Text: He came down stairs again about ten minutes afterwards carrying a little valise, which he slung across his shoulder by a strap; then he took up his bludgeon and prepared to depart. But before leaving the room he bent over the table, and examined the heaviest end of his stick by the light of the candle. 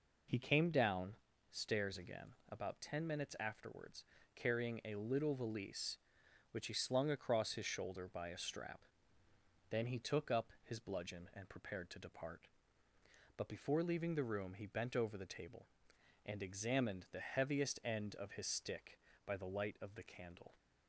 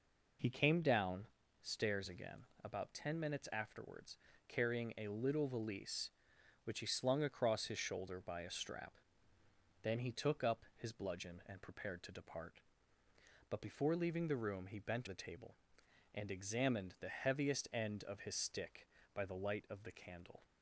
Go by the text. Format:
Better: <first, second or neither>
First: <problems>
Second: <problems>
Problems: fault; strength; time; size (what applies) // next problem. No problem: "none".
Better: first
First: pauses between "down" and "stairs"; slight; at 1.1 s; 0.34 s long // pauses between "again" and "about"; slight; at 2.3 s; 0.16 s long // pauses between "afterwards" and "carrying"; slight; at 4.0 s; 0.32 s long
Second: pauses between "down" and "stairs"; slight; at 1.2 s; 0.34 s long // pauses between "again" and "about"; slight; at 2.4 s; 0.18 s long // pauses between "afterwards" and "carrying"; slight; at 4.1 s; 0.32 s long // skips "over"; at 15.0 s